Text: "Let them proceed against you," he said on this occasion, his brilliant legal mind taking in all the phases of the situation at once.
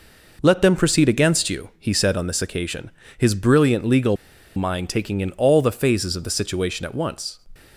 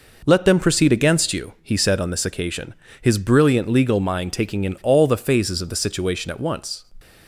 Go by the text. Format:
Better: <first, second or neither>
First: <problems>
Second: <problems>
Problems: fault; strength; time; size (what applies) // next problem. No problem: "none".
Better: second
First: pauses between "legal" and "mind"; at 4.1 s; 0.40 s long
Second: none